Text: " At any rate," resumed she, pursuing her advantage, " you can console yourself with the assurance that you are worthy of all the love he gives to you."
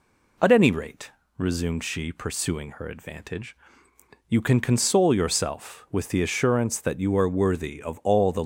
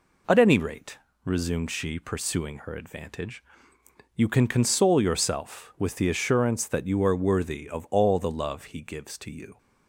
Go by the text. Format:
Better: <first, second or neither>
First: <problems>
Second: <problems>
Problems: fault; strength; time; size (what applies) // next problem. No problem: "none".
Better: second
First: stops before "love he gives to you"; at 8.4 s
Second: none